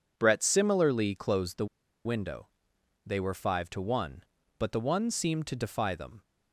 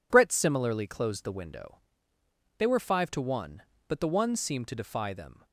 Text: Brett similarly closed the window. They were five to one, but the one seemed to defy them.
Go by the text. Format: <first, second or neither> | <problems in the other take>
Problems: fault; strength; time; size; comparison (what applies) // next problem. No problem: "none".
second | pauses between "the" and "window"; at 1.6 s; 0.39 s long